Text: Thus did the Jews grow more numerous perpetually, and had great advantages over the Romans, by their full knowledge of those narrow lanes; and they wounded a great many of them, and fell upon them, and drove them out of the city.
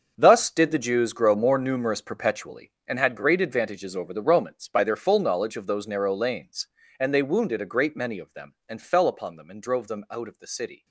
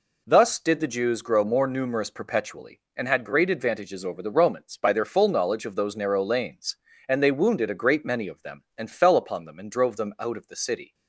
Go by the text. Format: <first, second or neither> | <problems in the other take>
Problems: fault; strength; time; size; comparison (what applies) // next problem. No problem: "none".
second | gets quieter; strong; throughout; 13 dB